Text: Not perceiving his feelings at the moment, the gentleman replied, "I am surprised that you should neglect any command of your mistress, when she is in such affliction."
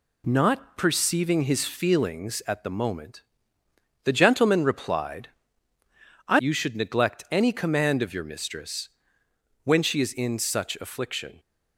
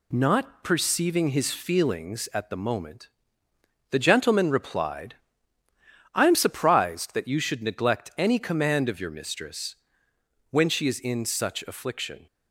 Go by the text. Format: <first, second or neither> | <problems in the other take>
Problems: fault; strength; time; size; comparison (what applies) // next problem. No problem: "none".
second | skips "am surprised that"; at 6.4 s